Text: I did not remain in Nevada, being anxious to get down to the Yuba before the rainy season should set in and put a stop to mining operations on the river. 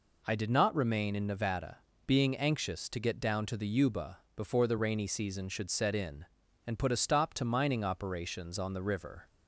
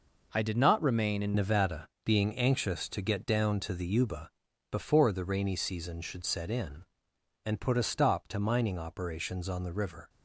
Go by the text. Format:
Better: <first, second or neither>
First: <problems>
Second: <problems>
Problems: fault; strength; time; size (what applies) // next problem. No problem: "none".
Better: first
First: pauses between "Yuba" and "before"; slight; at 4.1 s; 0.18 s long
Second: changes voice at "Nevada"; from 1.3 s on; 8.7 s long // pauses between "Yuba" and "before"; at 4.3 s; 0.40 s long